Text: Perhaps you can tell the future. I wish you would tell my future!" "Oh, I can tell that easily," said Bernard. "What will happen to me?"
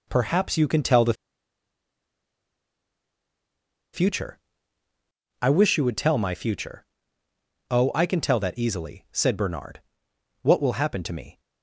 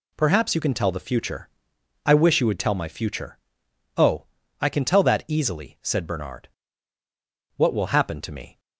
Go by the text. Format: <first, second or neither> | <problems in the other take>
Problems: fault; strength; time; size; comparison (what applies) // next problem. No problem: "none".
second | pauses between "the" and "future"; strong; at 1.1 s; 2.8 s long